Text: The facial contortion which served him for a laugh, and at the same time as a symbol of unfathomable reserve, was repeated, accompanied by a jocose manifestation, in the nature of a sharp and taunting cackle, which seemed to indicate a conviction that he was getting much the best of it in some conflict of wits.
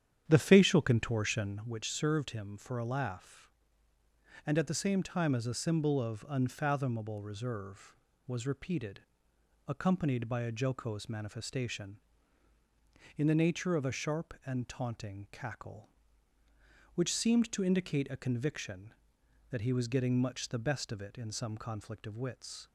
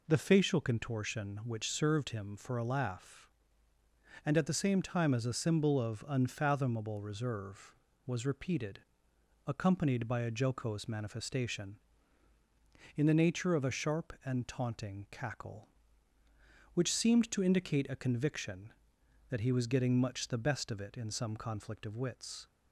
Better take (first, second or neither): second